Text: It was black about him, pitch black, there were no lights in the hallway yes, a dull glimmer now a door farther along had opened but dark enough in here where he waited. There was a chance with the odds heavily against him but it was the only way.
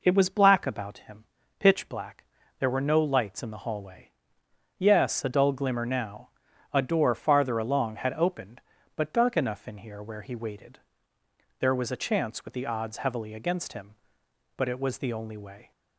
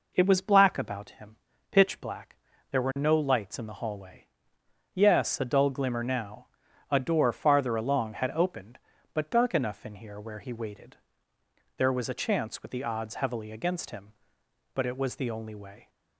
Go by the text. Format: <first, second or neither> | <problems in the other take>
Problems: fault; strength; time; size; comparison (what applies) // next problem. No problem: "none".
neither | pauses between "hallway" and "yes"; noticeable; the same in both // pauses between "now" and "a"; the same in both